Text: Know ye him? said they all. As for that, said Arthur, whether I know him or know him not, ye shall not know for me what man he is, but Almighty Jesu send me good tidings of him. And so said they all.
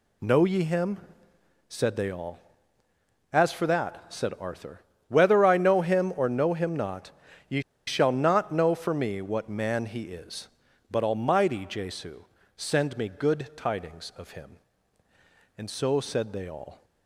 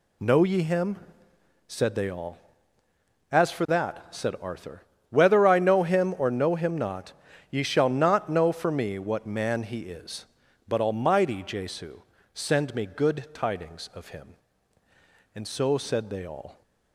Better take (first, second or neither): second